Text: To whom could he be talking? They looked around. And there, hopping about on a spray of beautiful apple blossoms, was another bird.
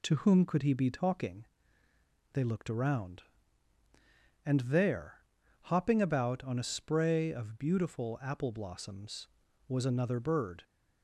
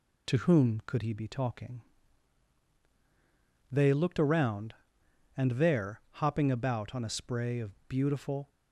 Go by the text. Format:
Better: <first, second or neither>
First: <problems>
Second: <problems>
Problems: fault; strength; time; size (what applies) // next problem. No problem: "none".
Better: first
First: none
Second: pauses between "of" and "beautiful"; slight; at 7.7 s; 0.16 s long // stops before "apple blossoms was another bird"; at 8.4 s